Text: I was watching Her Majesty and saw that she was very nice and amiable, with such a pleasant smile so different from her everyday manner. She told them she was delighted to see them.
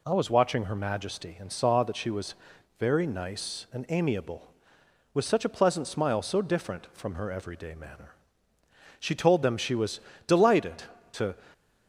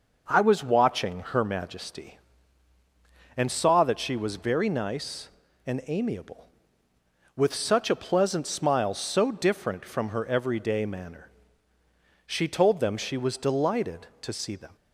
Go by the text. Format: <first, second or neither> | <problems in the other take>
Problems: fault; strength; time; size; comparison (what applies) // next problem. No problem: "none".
second | pauses between "was" and "very"; noticeable; at 2.3 s; 0.46 s long // pauses between "was" and "delighted"; slight; at 10.0 s; 0.26 s long // stops before "see them"; at 11.5 s